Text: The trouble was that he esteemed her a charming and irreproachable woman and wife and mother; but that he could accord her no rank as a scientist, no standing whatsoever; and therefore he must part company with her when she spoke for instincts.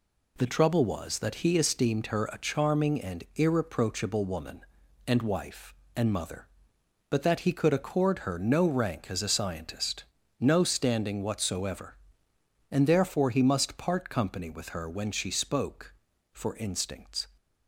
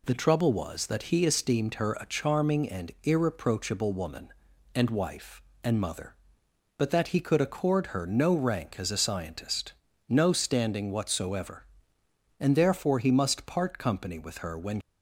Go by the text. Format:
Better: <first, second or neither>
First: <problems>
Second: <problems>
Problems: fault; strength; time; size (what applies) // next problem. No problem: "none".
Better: first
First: none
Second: stops before "she spoke for instincts"; at 14.8 s